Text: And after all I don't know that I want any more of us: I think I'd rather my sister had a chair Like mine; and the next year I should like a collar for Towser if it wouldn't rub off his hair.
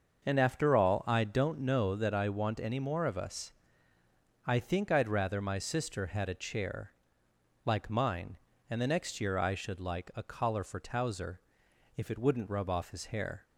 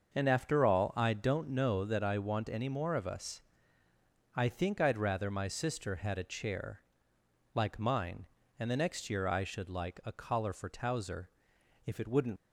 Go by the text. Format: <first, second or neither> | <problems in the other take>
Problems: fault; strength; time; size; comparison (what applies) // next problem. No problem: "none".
first | starts louder than the rest; until 1.1 s; 6.5 dB; also in the first // pauses between "chair" and "Like"; noticeable; at 6.8 s; 0.74 s long; noticeable in the first // pauses between "Towser" and "if"; noticeable; at 11.2 s; 0.56 s long; noticeable in the first // stops before "rub off his hair"; at 12.3 s